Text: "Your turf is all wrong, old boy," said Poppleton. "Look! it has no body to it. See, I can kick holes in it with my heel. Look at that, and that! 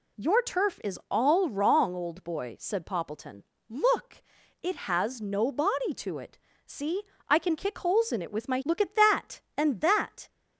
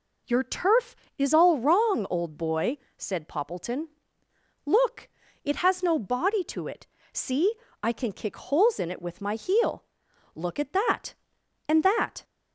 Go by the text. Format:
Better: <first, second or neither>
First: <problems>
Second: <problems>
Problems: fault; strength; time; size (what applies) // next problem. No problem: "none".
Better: second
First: skips "heel"; at 8.6 s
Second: none